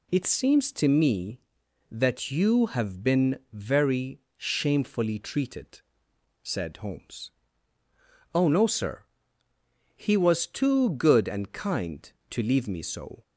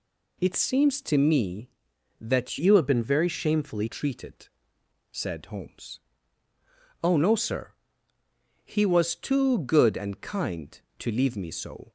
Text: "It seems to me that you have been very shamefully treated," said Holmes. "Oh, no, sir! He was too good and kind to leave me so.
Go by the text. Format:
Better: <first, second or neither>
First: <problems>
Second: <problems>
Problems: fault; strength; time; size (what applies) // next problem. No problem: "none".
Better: first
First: none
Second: changes voice from "you" to "shamefully"; from 2.5 to 3.8 s; 1.3 s long